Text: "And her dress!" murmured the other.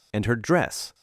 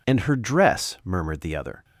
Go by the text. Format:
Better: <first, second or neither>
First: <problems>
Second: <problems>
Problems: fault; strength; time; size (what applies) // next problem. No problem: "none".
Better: second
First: stops before "murmured the other"; at 0.9 s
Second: none